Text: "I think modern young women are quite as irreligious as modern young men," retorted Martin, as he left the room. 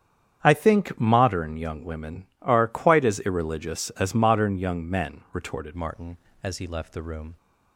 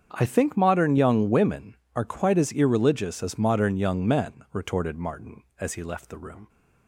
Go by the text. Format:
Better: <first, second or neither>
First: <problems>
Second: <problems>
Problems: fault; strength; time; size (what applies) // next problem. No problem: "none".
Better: second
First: starts louder than the rest; strong; until 1.4 s; 8.5 dB // changes voice at "Martin"; from 5.7 s on; 1.6 s long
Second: starts louder than the rest; strong; until 1.1 s; 7.5 dB